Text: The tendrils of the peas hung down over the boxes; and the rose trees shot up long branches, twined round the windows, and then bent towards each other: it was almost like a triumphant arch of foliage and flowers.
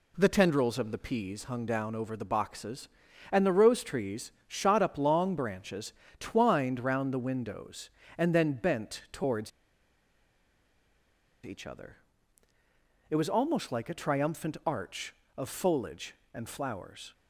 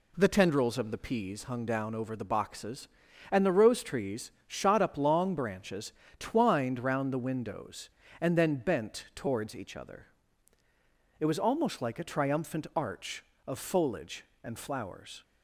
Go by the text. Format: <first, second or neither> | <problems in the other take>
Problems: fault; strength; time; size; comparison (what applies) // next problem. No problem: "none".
second | pauses between "trees" and "shot"; slight; at 4.3 s; 0.16 s long; slight in the second // pauses between "towards" and "each"; strong; at 9.5 s; 1.9 s long